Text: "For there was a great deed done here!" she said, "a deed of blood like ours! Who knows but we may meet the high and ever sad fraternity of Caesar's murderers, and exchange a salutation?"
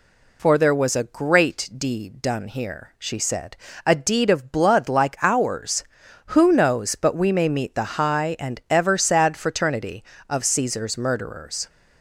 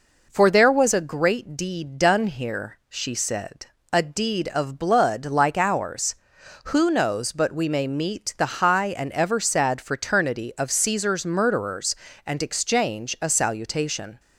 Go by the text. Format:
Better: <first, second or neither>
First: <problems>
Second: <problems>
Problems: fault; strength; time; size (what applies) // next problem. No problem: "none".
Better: second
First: stops before "and exchange a salutation"; at 11.6 s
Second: none